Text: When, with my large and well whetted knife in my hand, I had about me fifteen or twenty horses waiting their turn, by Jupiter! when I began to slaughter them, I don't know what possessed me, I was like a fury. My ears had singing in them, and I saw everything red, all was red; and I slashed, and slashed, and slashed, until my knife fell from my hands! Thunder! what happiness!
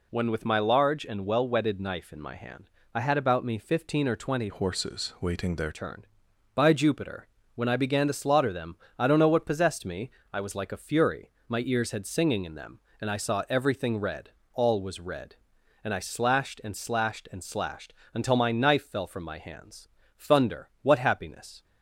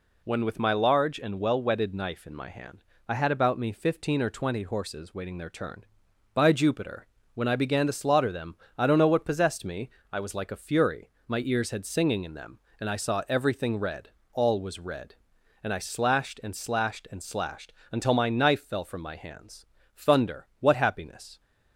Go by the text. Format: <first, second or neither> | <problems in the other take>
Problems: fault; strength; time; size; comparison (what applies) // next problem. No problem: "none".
second | changes voice from "horses" to "their"; from 4.4 to 5.7 s; 1.3 s long